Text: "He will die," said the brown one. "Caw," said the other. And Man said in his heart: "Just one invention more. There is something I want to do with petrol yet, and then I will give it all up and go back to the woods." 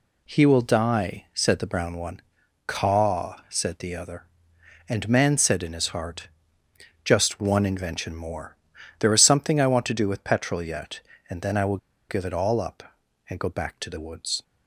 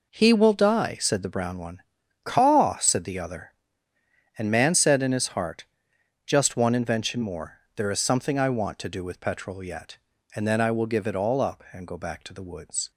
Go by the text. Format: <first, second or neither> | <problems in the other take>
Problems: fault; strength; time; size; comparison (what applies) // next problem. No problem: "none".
second | pauses between "will" and "give"; slight; at 11.7 s; 0.32 s long